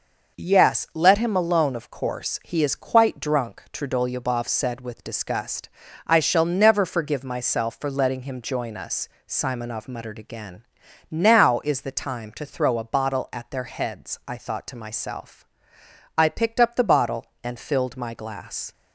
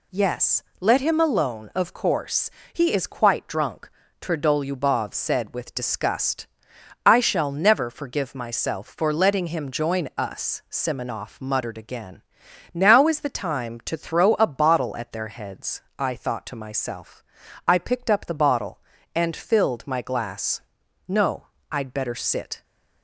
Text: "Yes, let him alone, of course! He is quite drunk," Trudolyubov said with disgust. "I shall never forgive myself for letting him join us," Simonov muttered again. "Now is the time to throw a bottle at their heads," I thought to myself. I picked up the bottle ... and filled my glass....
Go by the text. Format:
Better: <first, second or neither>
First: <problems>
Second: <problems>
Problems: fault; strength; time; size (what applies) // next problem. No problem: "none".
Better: first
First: none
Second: goes on to say "No I'd better sit"; from 21.0 s on; 1.5 s long